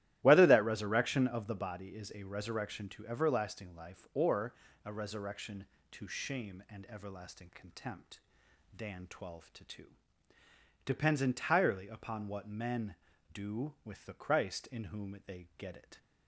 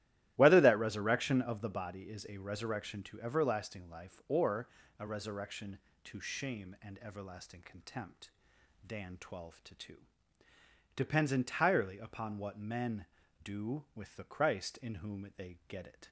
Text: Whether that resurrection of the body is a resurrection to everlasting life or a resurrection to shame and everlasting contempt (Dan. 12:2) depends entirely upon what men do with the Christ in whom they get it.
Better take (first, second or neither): neither